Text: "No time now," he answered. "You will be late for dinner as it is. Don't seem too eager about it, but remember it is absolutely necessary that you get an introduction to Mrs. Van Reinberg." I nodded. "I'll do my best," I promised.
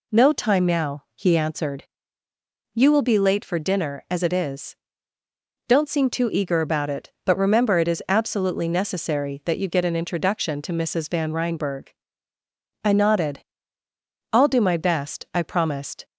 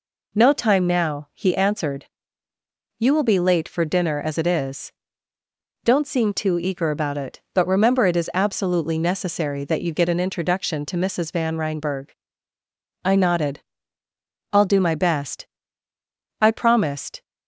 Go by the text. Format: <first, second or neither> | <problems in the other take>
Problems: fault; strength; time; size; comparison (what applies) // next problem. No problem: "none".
neither | none